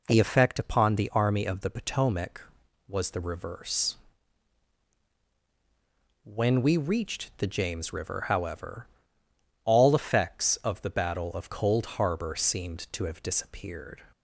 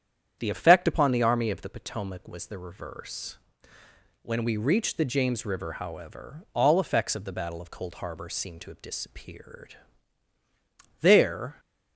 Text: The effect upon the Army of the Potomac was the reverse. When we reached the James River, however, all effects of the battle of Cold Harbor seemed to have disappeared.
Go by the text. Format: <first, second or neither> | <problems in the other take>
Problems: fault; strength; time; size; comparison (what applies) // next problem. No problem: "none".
first | starts louder than the rest; strong; until 1.4 s; 9 dB // goes on to say "There"; from 11.0 s on; 0.58 s long